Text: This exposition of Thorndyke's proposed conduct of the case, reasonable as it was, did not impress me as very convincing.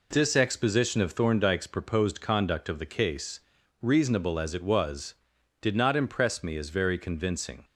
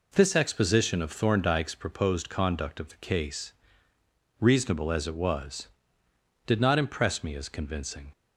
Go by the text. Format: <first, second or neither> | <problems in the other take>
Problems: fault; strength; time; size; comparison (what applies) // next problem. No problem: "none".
first | skips "very"; at 7.4 s